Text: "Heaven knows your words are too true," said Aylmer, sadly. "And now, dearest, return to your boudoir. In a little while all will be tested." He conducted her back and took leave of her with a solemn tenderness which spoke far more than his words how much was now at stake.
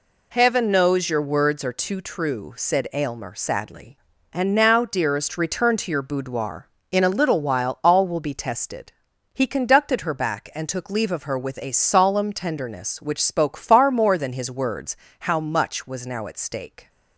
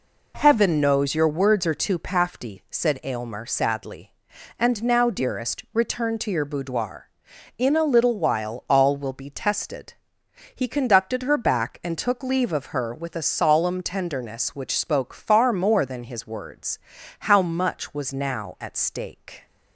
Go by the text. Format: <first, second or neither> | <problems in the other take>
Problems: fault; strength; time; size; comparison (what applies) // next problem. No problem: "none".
first | says "pafty" for "true"; at 1.9 s // pauses between "words" and "how"; at 16.7 s; 0.40 s long; slight in the first